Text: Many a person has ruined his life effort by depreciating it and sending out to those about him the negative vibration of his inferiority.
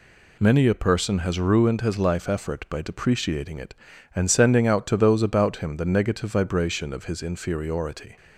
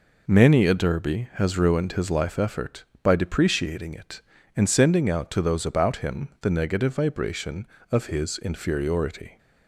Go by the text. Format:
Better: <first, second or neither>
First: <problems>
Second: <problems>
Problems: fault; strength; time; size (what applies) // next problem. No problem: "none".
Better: first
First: none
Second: says "derby" for "person"; at 0.7 s